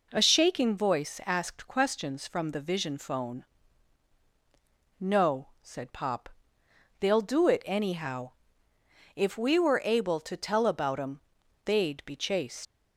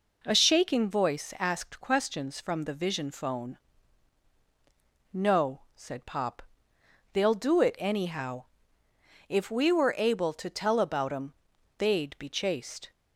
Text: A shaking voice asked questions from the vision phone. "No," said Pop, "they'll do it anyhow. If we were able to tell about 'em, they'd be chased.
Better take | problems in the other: second | leaves "chased" unfinished; at 12.6 s; 130 ms

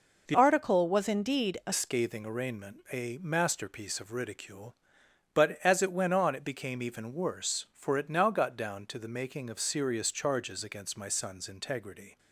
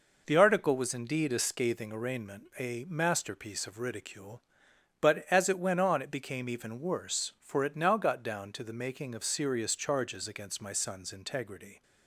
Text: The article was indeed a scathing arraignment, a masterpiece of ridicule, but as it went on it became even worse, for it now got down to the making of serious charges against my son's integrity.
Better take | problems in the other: second | changes voice from "article" to "a"; from 0.3 to 1.7 s; 1.4 s long

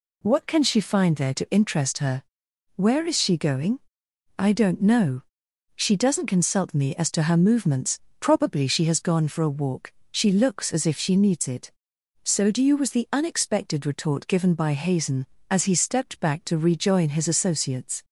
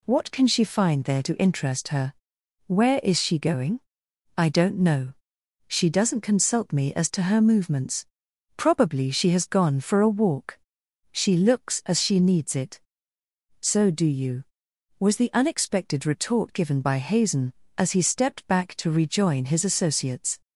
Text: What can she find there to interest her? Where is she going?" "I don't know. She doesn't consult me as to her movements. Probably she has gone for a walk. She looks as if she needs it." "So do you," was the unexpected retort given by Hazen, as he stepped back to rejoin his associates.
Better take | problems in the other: first | skips "if"; at 12.0 s

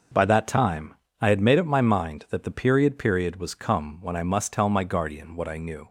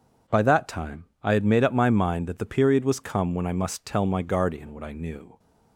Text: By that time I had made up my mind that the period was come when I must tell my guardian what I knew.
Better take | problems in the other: second | pauses between "time" and "I"; slight; at 0.9 s; 0.30 s long; slight in the second // says "period" twice; at 2.9 s

